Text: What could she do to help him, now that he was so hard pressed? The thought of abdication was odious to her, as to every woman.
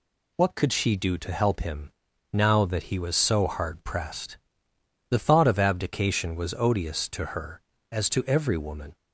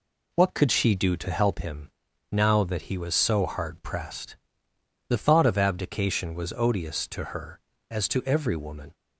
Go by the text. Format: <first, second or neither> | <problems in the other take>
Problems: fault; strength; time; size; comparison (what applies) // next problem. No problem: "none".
first | starts louder than the rest; slight; until 1.5 s; 3 dB